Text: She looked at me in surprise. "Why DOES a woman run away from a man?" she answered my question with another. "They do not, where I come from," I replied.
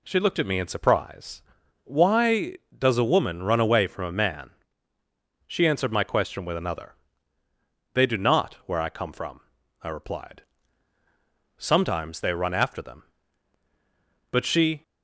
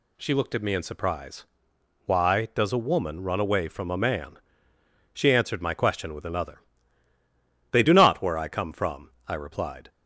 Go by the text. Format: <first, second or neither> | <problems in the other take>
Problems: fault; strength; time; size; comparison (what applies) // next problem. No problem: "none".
second | goes on to say "Sometimes they run after them But she"; strong; from 11.5 s on; 3.2 s long